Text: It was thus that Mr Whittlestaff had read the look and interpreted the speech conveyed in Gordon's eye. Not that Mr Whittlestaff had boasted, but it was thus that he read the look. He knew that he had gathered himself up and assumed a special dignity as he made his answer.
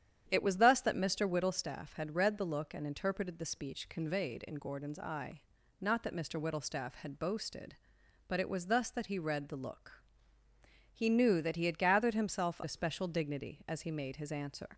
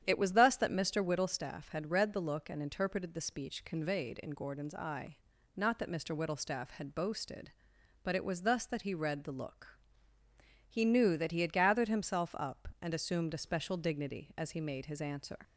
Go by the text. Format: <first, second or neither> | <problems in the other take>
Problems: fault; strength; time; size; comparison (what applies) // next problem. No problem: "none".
second | starts louder than the rest; strong; until 1.2 s; 9.5 dB; strong in the second // skips "up and assumed"; at 12.6 s